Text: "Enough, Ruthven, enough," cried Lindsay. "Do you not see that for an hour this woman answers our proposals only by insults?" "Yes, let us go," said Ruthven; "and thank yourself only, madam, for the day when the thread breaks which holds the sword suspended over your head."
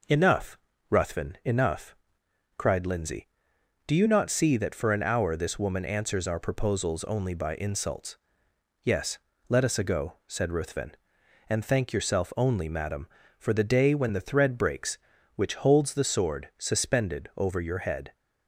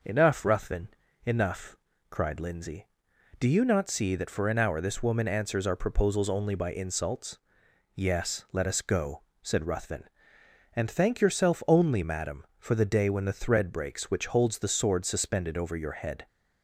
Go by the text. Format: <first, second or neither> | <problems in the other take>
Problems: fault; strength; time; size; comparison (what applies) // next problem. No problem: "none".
second | says "ago" for "go"; at 9.7 s